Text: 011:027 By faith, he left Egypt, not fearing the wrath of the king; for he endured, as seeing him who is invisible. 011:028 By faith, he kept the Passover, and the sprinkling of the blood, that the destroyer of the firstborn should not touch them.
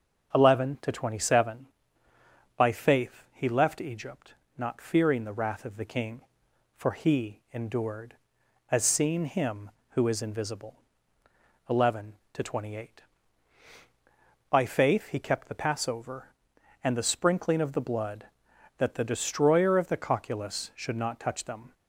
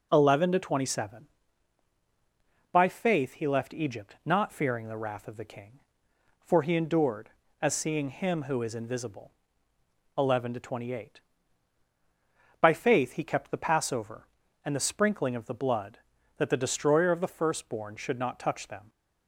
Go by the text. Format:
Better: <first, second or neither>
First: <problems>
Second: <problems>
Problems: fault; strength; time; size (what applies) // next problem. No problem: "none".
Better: second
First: starts louder than the rest; until 1.3 s; 6.5 dB // says "cocculus" for "firstborn"; at 19.9 s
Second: none